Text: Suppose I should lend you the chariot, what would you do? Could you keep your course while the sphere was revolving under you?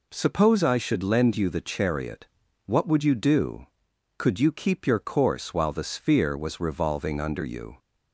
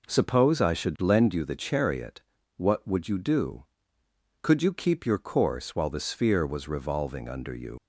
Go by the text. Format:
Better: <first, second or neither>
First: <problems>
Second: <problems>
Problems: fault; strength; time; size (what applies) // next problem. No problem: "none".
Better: first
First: none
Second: leaves "you" unfinished; at 7.7 s; 95 ms